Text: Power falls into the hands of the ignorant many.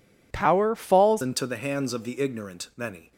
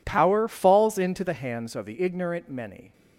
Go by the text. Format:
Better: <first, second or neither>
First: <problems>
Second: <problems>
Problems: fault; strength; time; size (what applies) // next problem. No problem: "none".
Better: second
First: changes voice at "into"; from 1.2 s on; 1.9 s long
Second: none